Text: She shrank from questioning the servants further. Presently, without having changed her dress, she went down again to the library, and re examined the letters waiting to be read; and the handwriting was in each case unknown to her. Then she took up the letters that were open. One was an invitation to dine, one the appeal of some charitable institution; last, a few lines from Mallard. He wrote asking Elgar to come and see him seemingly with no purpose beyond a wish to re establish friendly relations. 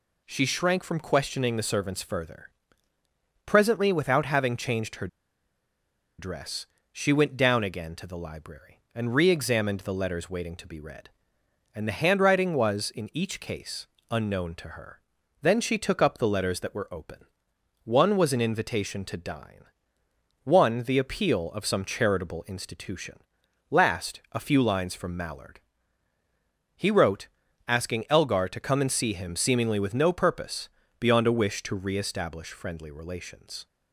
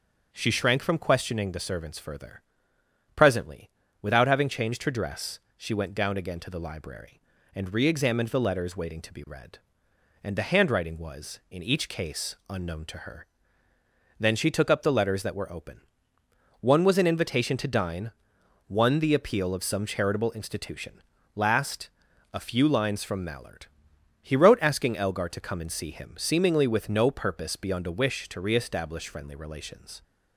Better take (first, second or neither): second